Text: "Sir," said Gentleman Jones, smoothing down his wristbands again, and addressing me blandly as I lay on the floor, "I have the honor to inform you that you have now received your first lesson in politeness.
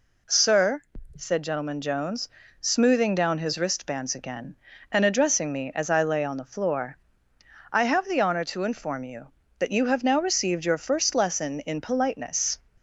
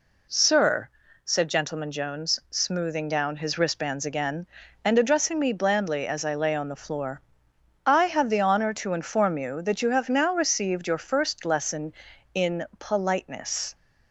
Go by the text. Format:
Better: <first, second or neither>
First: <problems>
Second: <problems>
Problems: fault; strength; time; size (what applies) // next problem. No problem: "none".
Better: second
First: skips "blandly"; at 5.7 s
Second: none